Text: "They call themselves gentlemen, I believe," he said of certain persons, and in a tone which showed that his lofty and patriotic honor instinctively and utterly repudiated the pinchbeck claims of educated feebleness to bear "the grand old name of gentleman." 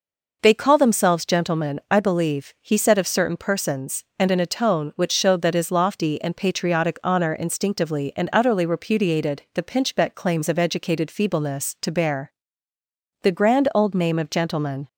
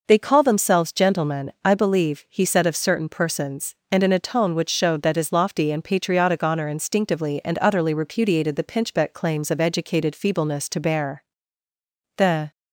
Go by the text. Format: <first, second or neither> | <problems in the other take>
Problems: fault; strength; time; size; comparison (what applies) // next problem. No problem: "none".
first | pauses between "bear" and "the"; noticeable; at 11.2 s; 0.94 s long; noticeable in the first // stops before "grand old name of gentleman"; at 12.5 s